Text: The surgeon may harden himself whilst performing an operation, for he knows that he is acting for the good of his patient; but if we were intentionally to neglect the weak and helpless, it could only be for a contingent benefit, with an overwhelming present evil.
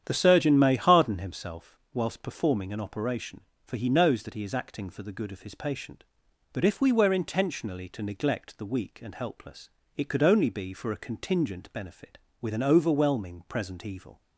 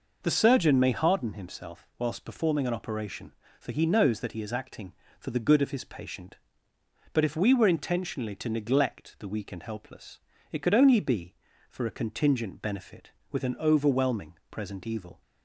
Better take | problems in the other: second | starts louder than the rest; strong; until 1.4 s; 9.5 dB // pauses between "himself" and "whilst"; slight; at 1.7 s; 0.16 s long

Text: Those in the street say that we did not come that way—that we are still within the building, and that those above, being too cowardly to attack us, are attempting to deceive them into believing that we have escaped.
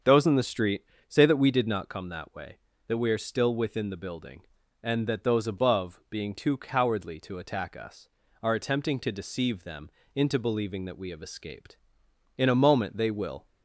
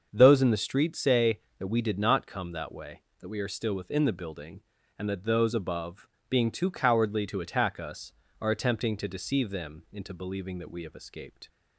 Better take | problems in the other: second | starts louder than the rest; until 1.2 s; 7 dB; also in the second // pauses between "street" and "say"; slight; at 0.8 s; 0.24 s long // pauses between "them" and "into"; slight; at 9.8 s; 0.26 s long // goes on to say "In a moment they will"; noticeable; from 12.3 s on; 1.0 s long

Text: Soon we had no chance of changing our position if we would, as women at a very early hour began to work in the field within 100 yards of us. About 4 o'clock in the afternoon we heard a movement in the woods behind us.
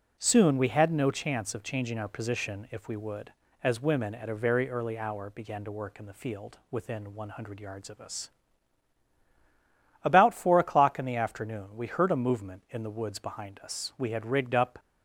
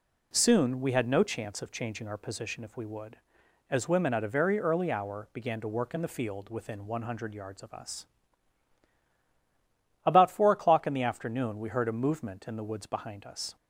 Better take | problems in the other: second | goes on to say "We had rigged up"; noticeable; from 13.9 s on; 0.84 s long

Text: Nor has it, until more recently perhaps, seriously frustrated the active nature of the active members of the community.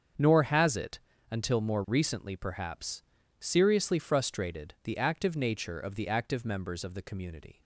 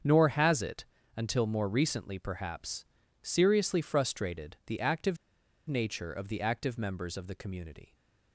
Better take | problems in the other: first | starts louder than the rest; strong; until 1.3 s; 7 dB; strong in the first // pauses between "active" and "nature"; noticeable; at 5.1 s; 0.51 s long

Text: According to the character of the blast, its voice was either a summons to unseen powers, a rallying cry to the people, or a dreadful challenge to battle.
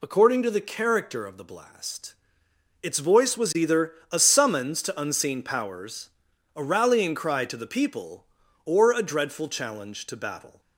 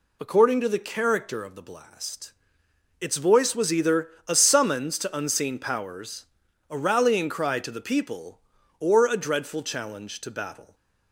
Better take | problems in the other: neither | pauses between "either" and "a"; slight; the same in both

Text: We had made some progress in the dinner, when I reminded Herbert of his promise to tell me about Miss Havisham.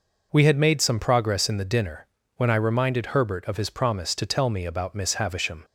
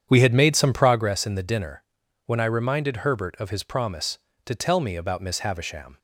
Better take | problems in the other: first | starts louder than the rest; strong; until 1.1 s; 8.5 dB

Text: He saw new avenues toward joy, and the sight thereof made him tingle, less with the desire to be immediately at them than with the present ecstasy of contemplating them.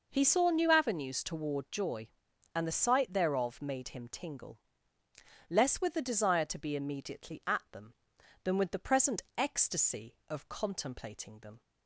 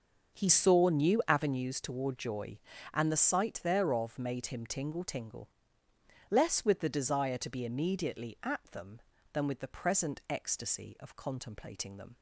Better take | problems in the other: first | starts louder than the rest; until 1.4 s; 6.5 dB // says "tingle" twice; at 5.0 s

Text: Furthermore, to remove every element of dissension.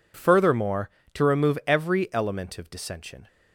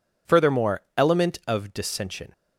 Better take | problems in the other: first | skips "to remove every"; at 0.8 s

